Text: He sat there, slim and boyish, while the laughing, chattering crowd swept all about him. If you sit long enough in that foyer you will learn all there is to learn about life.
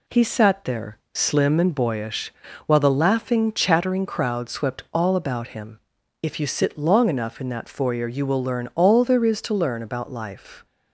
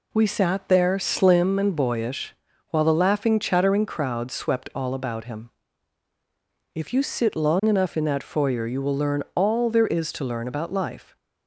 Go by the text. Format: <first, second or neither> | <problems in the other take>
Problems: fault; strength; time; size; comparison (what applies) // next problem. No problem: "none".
first | says "We" for "He"; at 0.1 s